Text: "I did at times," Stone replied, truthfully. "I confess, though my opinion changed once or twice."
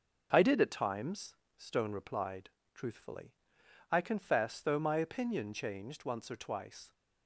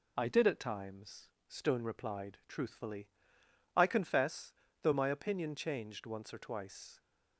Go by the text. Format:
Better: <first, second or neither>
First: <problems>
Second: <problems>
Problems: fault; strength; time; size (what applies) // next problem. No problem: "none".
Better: neither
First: none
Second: none